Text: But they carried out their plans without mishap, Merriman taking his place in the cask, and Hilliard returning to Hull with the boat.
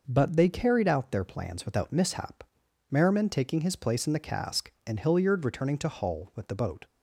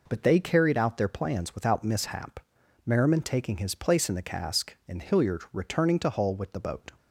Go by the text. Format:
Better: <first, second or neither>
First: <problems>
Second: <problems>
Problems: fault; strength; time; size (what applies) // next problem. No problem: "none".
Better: neither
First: none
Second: none